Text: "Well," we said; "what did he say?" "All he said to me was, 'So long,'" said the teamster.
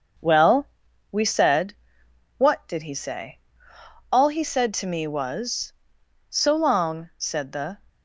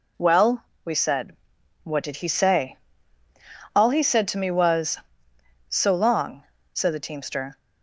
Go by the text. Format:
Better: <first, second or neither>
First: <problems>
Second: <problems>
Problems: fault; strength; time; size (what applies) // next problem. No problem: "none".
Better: second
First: starts louder than the rest; until 1.6 s; 6.5 dB // stops before "teamster"; at 7.8 s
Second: none